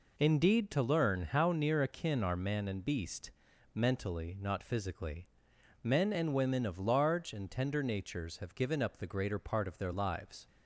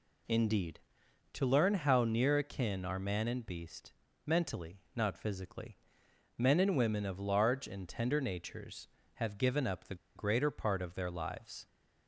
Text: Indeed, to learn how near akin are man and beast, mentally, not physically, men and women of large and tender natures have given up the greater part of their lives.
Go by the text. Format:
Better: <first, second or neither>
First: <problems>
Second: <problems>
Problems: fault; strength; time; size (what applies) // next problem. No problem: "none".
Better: first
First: none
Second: pauses between "the" and "greater"; slight; at 9.9 s; 0.21 s long